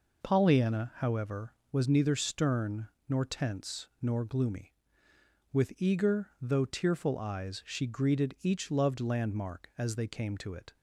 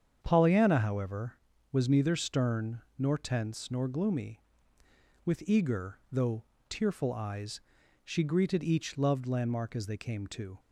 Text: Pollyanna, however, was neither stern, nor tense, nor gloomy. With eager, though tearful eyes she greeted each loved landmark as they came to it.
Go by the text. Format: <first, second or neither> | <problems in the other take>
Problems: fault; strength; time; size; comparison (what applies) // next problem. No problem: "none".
first | starts louder than the rest; strong; until 1.2 s; 8 dB // pauses between "though" and "tearful"; slight; at 6.4 s; 0.26 s long // pauses between "eyes" and "she"; at 7.5 s; 0.44 s long // stops before "it"; at 10.5 s